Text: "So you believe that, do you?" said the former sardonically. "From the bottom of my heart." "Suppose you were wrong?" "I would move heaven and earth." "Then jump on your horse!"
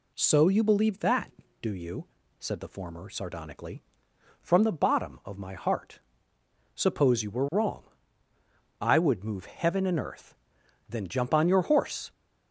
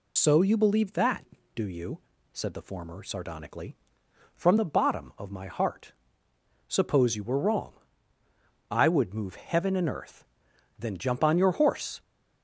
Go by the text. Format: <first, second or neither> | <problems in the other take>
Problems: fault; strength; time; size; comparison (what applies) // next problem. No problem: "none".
first | loses the start of "So"; at 0.1 s; 70 ms